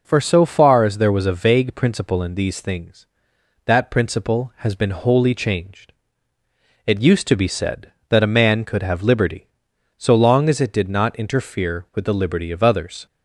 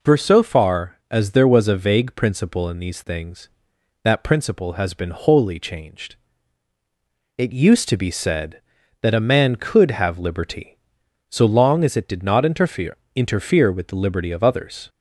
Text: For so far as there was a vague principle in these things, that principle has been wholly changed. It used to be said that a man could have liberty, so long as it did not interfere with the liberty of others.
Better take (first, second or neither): first